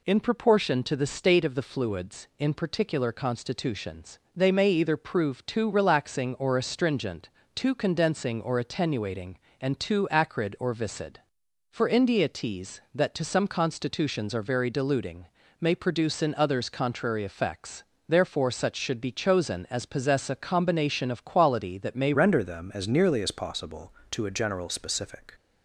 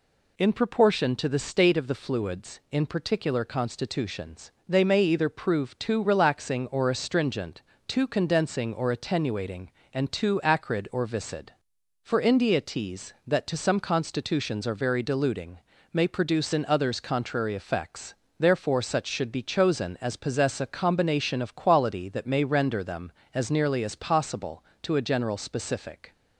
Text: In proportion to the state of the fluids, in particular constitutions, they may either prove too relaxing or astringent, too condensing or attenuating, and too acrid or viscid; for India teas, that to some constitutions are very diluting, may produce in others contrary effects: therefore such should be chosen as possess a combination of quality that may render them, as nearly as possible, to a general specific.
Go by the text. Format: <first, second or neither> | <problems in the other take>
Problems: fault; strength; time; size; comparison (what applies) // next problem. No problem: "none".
second | changes voice at "render"; from 22.1 s on; 3.2 s long